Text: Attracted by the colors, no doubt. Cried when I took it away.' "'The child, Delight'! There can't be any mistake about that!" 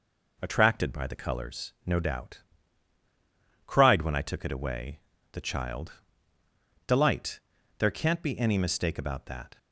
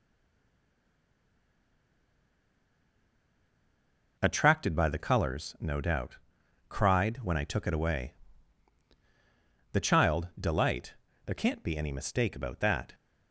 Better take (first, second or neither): first